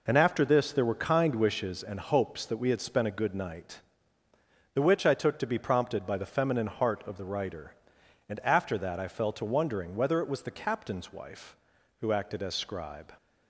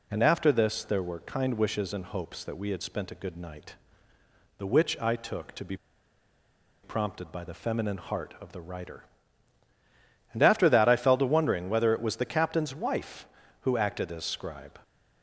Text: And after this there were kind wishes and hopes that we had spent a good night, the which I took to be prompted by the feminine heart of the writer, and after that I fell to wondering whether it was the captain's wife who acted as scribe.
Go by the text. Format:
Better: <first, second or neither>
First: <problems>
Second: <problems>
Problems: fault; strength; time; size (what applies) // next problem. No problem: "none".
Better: first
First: none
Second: pauses between "be" and "prompted"; at 5.7 s; 1.0 s long